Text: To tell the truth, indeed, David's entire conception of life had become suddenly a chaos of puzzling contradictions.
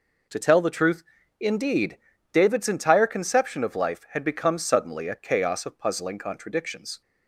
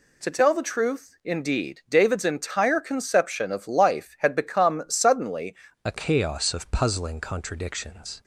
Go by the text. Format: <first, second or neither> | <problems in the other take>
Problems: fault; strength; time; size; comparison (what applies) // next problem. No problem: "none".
first | changes voice at "a"; from 5.8 s on; 2.4 s long